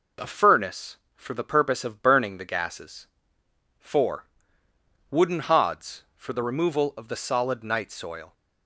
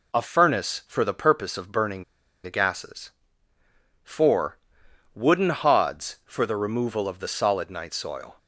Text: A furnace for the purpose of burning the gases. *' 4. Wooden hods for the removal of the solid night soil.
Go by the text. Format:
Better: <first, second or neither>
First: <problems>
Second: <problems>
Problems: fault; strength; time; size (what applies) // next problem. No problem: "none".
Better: first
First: none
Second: pauses between "burning" and "the"; at 2.0 s; 0.41 s long